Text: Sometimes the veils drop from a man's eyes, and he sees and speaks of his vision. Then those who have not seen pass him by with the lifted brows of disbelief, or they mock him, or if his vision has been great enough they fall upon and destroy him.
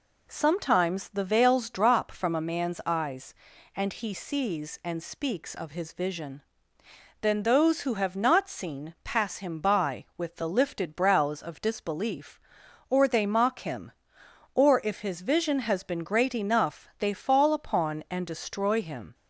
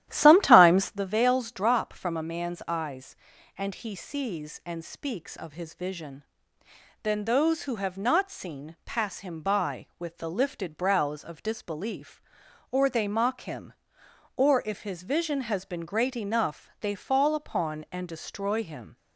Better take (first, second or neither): first